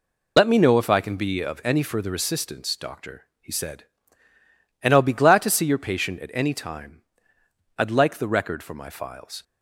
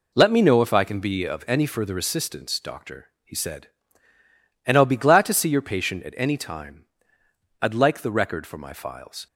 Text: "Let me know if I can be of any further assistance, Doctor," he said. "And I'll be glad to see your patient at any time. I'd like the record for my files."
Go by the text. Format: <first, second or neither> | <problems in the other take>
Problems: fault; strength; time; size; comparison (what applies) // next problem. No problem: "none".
second | loses the start of "Let"; at 0.3 s; 55 ms